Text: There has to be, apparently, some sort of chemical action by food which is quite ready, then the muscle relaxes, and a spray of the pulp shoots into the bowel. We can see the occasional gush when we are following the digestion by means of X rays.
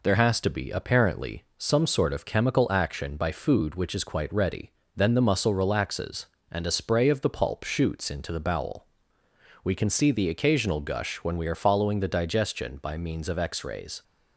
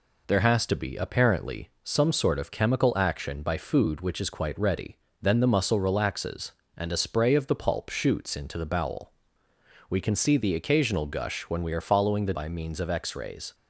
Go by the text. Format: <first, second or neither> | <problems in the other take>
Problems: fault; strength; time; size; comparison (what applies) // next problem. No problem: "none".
first | skips "digestion"; at 12.3 s